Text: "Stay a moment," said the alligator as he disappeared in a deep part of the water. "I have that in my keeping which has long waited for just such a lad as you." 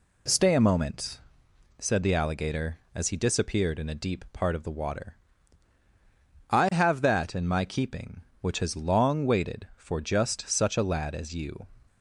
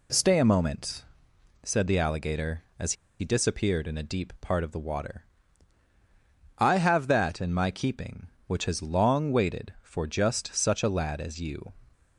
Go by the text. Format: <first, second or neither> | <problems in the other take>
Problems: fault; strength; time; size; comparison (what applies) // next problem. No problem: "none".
first | pauses between "as" and "he"; slight; at 2.9 s; 0.26 s long